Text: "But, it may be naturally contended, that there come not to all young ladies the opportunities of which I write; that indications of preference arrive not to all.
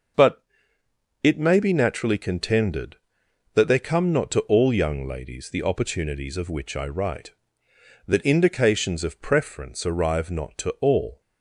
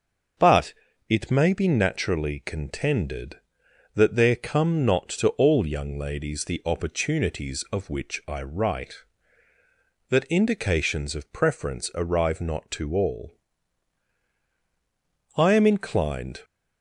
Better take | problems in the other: first | starts louder than the rest; until 1.7 s; 6.5 dB; also in the first // goes on to say "I am inclined"; noticeable; from 15.3 s on; 1.0 s long

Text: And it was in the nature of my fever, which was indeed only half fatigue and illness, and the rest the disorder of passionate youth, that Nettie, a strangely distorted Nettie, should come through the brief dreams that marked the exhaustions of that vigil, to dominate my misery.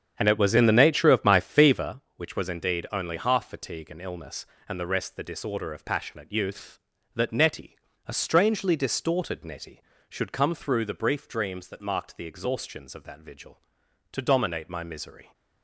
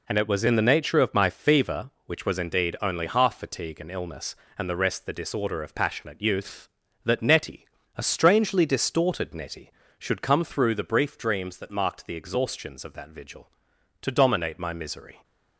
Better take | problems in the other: second | starts louder than the rest; strong; until 1.9 s; 8 dB

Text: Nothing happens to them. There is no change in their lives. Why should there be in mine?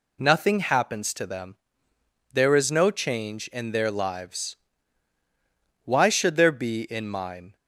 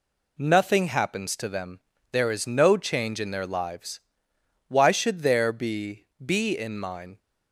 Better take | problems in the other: first | says "be" twice; at 6.2 s

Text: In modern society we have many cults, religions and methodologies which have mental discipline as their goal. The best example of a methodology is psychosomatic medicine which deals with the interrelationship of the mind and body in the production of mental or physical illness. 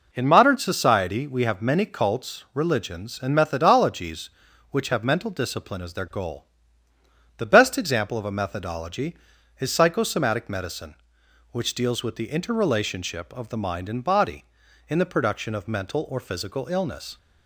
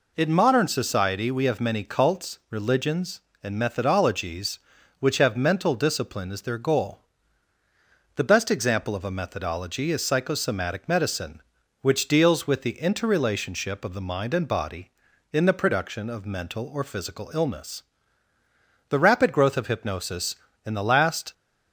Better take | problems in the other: first | goes on to say "The rapid growth of hypnosis in the last"; strong; from 18.8 s on; 2.4 s long

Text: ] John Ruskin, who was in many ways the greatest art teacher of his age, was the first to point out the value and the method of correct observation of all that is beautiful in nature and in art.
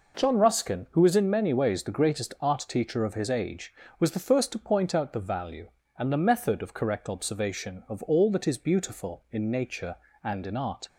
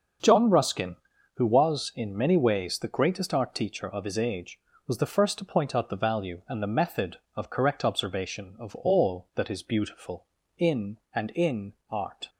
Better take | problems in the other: first | starts louder than the rest; until 1.6 s; 6.5 dB // skips "nature"; at 11.0 s // pauses between "in" and "art"; slight; at 11.7 s; 0.16 s long

